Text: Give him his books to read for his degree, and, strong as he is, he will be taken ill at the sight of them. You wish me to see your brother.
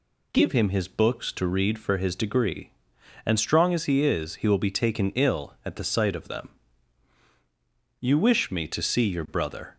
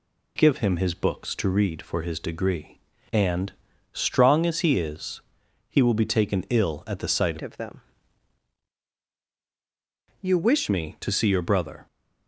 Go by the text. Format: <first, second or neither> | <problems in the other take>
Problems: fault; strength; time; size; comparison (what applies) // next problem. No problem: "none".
first | changes voice from "of" to "wish"; from 7.4 to 10.6 s; 3.2 s long